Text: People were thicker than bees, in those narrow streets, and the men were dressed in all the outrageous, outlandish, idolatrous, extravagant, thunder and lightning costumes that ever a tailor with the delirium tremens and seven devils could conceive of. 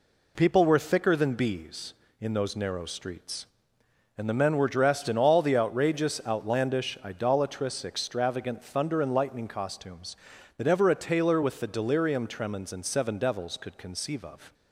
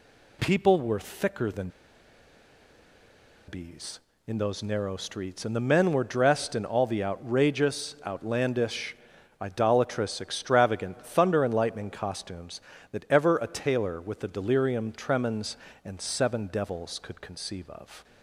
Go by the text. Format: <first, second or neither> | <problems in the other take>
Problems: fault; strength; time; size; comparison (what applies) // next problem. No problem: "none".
first | pauses between "than" and "bees"; strong; at 1.6 s; 1.7 s long